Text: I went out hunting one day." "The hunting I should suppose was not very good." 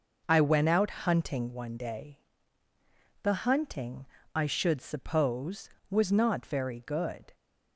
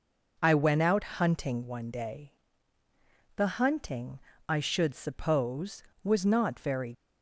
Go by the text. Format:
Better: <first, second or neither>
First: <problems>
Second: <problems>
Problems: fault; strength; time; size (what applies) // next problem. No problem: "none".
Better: first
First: pauses between "hunting" and "I"; slight; at 4.0 s; 0.28 s long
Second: pauses between "hunting" and "I"; slight; at 4.2 s; 0.28 s long // stops before "good"; at 6.9 s